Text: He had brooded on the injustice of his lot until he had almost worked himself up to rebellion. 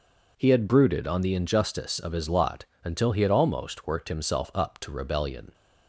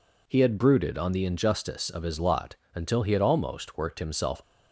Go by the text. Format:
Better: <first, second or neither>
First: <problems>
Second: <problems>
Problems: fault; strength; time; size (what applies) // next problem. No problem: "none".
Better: first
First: pauses between "lot" and "until"; slight; at 2.6 s; 0.18 s long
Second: pauses between "lot" and "until"; slight; at 2.5 s; 0.18 s long // stops before "up to rebellion"; at 4.4 s